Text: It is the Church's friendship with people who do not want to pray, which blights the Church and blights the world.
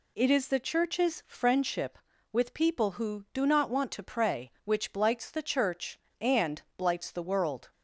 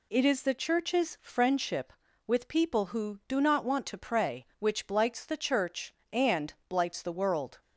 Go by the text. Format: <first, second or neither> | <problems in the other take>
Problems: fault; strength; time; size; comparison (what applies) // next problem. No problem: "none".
neither | pauses between "and" and "blights"; slight; the same in both